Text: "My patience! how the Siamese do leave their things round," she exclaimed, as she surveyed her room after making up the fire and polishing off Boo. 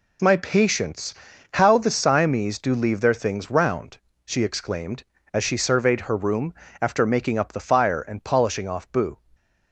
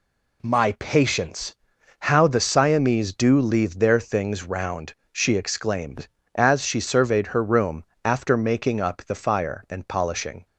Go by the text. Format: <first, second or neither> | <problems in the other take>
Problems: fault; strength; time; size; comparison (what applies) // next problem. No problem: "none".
first | pauses between "room" and "after"; slight; at 7.8 s; 0.22 s long; slight in the first // stops before "off Boo"; at 10.4 s